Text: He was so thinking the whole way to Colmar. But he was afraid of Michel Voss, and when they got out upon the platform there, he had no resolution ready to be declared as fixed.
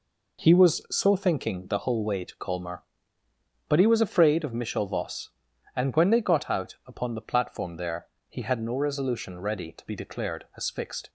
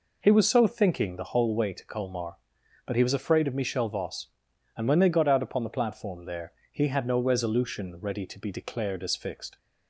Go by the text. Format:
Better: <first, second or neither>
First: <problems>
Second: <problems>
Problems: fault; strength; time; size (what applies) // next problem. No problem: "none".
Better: neither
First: none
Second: none